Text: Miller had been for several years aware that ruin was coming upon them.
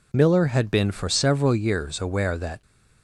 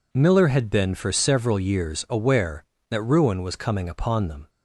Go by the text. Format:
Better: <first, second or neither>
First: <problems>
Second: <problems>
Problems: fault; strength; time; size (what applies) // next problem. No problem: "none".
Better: second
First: stops before "ruin was coming upon them"; at 2.6 s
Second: none